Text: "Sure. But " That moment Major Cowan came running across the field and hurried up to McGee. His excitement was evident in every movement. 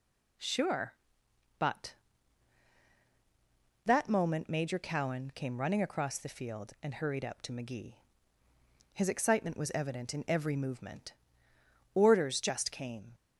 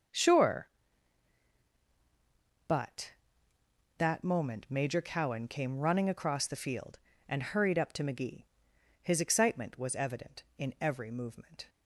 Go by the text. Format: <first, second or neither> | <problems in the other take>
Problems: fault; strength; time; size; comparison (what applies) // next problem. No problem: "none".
second | goes on to say "Orders just came"; noticeable; from 11.9 s on; 1.2 s long